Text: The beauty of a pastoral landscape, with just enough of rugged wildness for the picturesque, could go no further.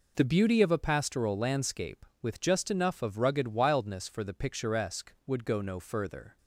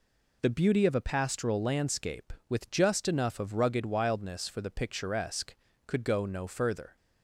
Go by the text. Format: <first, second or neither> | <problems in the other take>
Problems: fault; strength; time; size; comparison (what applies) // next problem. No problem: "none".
second | says "would" for "could"; at 5.2 s